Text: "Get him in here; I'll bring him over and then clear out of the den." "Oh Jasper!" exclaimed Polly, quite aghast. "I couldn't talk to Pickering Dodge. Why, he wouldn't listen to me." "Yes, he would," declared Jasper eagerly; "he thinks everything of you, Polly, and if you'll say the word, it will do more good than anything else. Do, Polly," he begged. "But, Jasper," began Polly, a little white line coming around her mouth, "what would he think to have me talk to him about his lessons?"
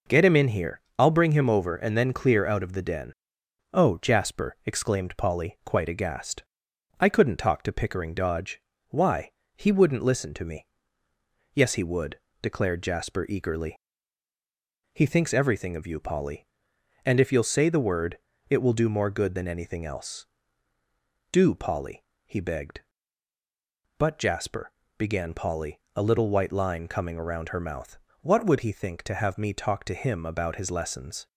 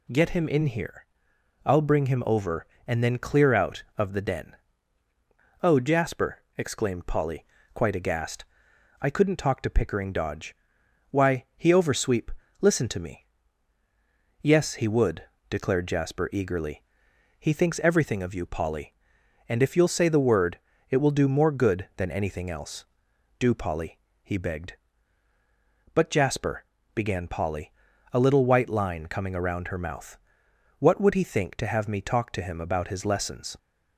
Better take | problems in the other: first | says "oversweep" for "wouldn't"; at 11.7 s

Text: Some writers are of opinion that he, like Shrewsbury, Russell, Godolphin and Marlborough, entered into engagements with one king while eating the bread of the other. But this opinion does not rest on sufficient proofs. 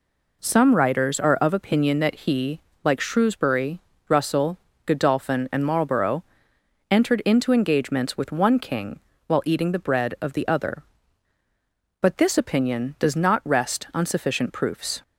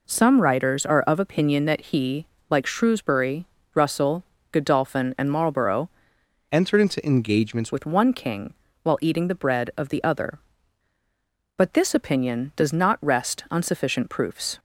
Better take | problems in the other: first | changes voice from "entered" to "engagements"; from 6.5 to 7.7 s; 1.2 s long // pauses between "king" and "while"; slight; at 8.5 s; 0.28 s long; slight in the first

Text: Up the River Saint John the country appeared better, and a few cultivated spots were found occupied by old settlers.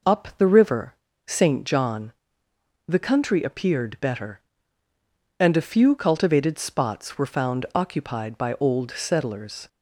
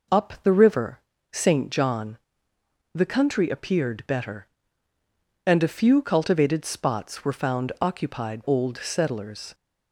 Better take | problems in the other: first | pauses between "River" and "Saint"; slight; at 1.0 s; 0.32 s long; slight in the first // pauses between "John" and "the"; noticeable; at 2.1 s; 0.78 s long; noticeable in the first // skips "by"; at 8.4 s

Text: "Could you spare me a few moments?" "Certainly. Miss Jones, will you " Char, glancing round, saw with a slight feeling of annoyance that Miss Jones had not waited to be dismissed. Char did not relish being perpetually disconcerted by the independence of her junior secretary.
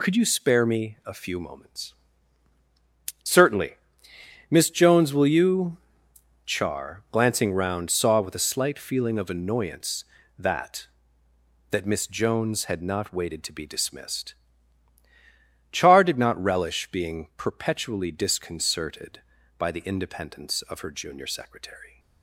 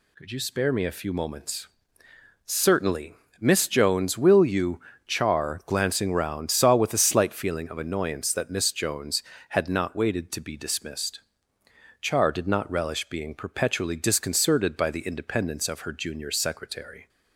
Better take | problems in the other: second | says "that" twice; at 11.6 s

